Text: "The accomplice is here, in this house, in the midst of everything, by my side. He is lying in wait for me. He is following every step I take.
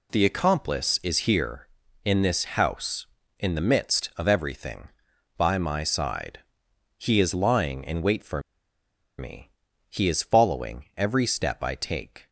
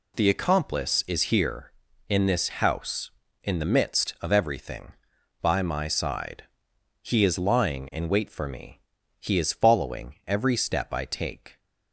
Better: second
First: pauses between "for" and "me"; noticeable; at 8.3 s; 0.78 s long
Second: none

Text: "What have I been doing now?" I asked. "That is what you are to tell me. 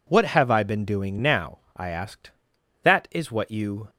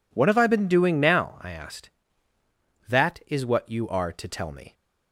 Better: second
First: stops before "are to tell me"; at 3.8 s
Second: none

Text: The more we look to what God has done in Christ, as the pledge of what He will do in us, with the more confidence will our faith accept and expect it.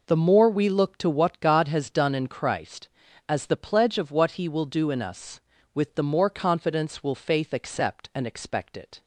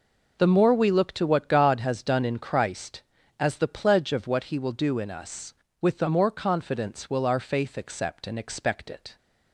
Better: second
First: skips "our"; at 7.1 s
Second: none

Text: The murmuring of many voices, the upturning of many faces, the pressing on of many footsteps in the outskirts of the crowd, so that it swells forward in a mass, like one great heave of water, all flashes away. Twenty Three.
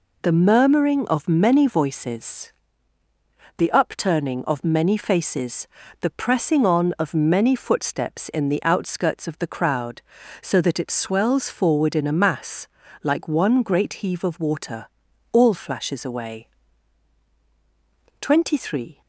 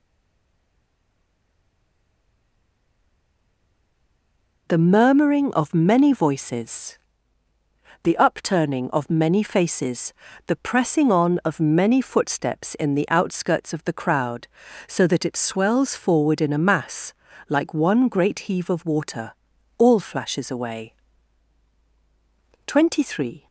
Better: first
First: none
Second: stays silent before the first word; strong; until 4.6 s; 4.6 s long

